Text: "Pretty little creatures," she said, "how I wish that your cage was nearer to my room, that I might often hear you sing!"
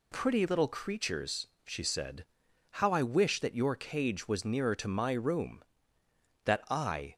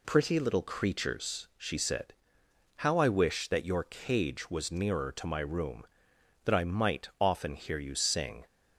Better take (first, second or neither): second